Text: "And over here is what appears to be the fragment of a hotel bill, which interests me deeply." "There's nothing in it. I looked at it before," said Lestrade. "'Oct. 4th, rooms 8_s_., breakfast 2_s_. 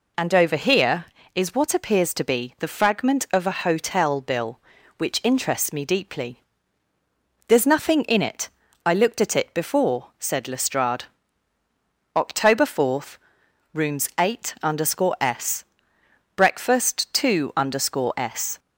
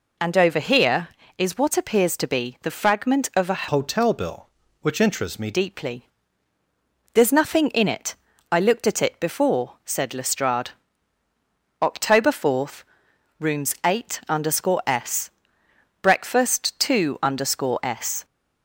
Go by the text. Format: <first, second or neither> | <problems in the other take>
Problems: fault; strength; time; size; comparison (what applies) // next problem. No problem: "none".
first | changes voice from "hotel" to "me"; from 3.6 to 5.5 s; 1.9 s long